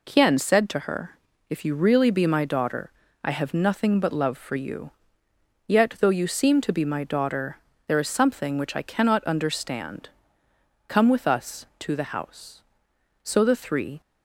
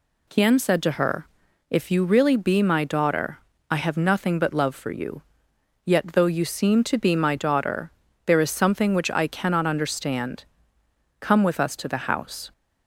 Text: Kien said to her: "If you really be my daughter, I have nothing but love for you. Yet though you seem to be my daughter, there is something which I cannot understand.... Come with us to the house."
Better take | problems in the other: second | goes on to say "So the three"; noticeable; from 13.2 s on; 0.78 s long

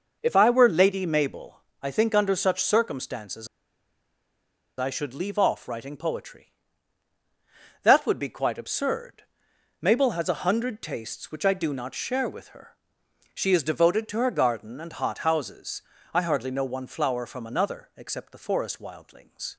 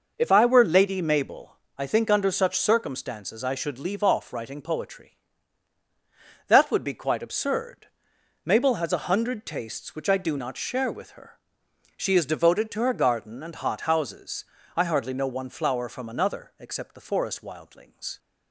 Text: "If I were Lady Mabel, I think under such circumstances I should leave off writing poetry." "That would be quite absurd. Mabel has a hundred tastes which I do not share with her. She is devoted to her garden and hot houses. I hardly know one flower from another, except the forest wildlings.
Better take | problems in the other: second | pauses between "circumstances" and "I"; strong; at 3.4 s; 1.3 s long

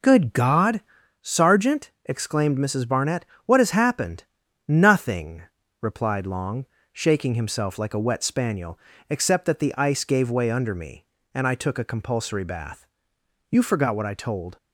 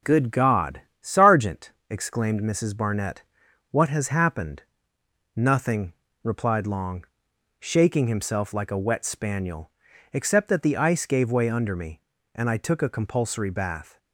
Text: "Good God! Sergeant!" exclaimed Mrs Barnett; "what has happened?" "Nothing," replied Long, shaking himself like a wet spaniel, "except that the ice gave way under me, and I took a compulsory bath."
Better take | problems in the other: second | goes on to say "You forgot what I told"; noticeable; from 13.5 s on; 1.0 s long

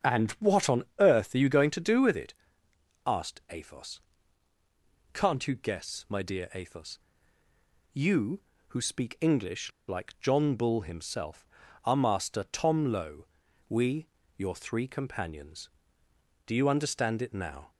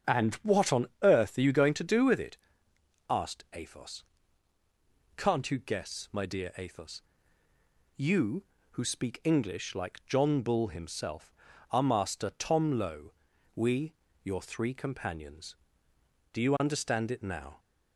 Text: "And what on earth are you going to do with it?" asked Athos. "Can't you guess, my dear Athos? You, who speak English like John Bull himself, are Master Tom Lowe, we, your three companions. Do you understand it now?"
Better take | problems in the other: second | starts louder than the rest; strong; until 1.2 s; 8 dB; strong in the second // pauses between "on" and "earth"; slight; at 0.8 s; 0.16 s long; slight in the second // pauses between "English" and "like"; slight; at 9.7 s; 0.17 s long

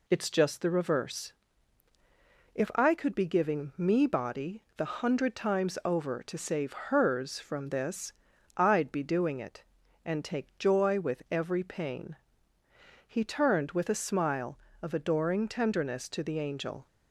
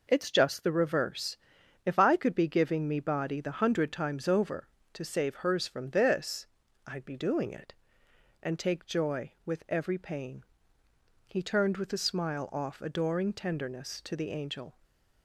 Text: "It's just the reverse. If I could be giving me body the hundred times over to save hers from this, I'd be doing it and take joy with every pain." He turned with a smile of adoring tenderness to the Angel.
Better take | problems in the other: first | says "off" for "of"; at 12.5 s // stays silent after the last word; slight; from 14.7 s on; 0.5 s long

